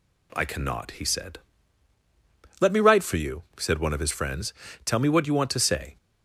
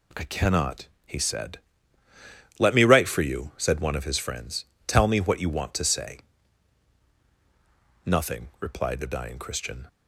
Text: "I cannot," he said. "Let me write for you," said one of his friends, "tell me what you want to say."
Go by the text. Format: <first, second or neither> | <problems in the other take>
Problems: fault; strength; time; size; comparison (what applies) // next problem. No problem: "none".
first | goes on to say "Nothing replied the dying Christian"; strong; from 8.0 s on; 1.8 s long